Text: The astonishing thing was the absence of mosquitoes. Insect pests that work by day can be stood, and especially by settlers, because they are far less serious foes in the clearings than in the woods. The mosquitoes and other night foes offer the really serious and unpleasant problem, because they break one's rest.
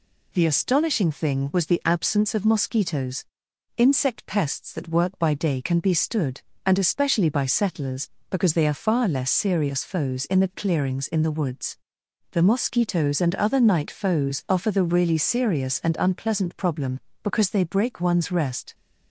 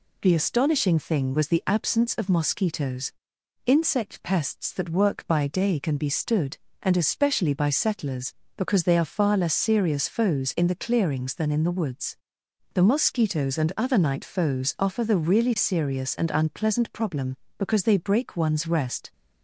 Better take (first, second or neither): second